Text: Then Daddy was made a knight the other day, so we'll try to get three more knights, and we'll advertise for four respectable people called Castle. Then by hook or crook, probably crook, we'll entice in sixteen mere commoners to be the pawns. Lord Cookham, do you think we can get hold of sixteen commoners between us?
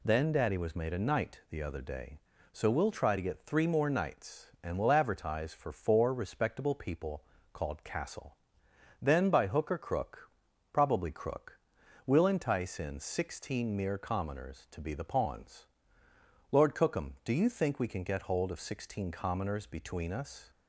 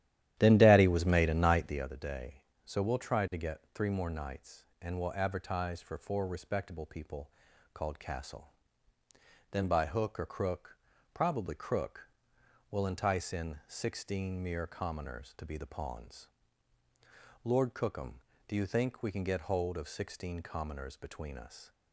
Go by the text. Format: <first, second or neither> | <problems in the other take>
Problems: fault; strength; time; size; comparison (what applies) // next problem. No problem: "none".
first | starts louder than the rest; strong; until 1.9 s; 12 dB // pauses between "people" and "called"; at 7.2 s; 0.44 s long; slight in the first